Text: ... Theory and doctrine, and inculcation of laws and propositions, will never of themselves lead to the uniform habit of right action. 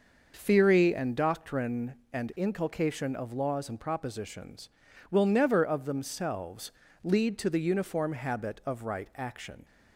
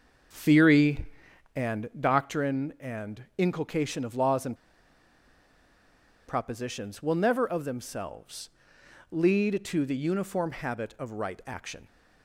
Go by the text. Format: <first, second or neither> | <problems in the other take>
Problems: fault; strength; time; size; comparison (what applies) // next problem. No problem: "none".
first | starts louder than the rest; noticeable; until 1.8 s; 6 dB // pauses between "and" and "propositions"; strong; at 4.5 s; 1.7 s long // pauses between "themselves" and "lead"; noticeable; at 8.4 s; 0.62 s long; slight in the first